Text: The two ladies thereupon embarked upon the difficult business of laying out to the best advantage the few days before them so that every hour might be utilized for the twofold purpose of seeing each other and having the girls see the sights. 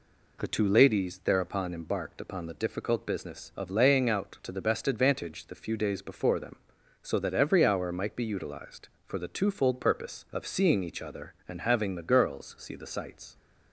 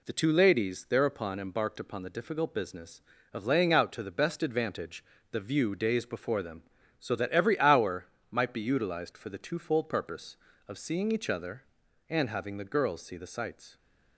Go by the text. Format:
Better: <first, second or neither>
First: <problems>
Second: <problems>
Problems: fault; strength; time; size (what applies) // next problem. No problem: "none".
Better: first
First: none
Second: pauses between "advantage" and "the"; slight; at 5.0 s; 0.28 s long // says "view" for "few"; at 5.3 s // pauses between "hour" and "might"; slight; at 8.0 s; 0.22 s long